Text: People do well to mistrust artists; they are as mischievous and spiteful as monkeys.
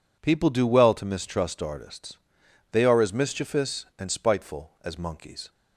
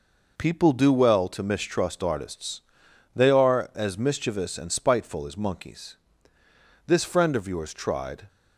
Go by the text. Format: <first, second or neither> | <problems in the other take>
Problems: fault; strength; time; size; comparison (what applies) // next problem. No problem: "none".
first | goes on to say "This friend of yours tried"; from 6.8 s on; 1.4 s long